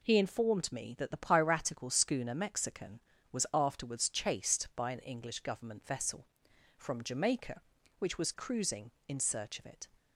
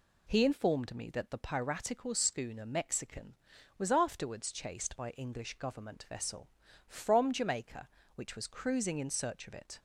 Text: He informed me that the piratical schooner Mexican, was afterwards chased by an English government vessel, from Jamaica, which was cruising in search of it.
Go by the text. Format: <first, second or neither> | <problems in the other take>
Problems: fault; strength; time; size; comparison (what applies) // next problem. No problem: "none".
first | skips "an"; at 5.0 s